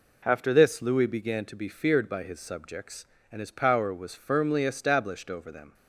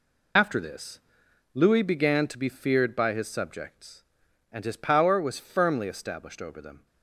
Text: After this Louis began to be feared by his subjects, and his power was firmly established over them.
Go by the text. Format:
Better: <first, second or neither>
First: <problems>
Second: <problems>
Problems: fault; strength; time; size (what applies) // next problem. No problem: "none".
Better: first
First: none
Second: loses the start of "After"; at 0.3 s; 85 ms // pauses between "this" and "Louis"; noticeable; at 0.9 s; 0.54 s long